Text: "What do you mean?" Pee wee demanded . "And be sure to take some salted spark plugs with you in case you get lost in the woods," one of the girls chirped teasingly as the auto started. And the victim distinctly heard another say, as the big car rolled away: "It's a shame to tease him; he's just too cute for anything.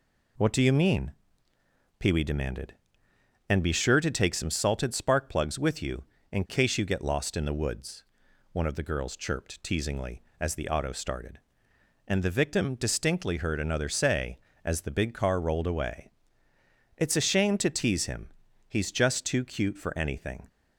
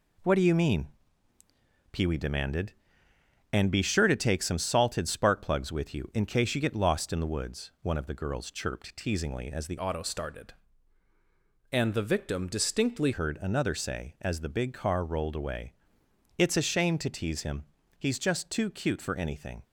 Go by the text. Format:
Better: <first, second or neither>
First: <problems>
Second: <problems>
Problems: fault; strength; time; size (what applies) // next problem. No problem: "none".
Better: first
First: none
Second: changes voice from "auto" to "distinctly"; from 9.7 to 13.1 s; 3.4 s long